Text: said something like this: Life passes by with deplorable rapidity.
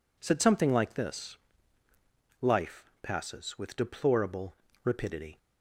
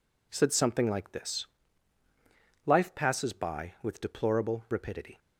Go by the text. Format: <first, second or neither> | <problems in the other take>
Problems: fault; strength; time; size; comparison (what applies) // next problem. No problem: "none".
second | skips "by"; at 3.5 s // pauses between "deplorable" and "rapidity"; slight; at 4.5 s; 0.28 s long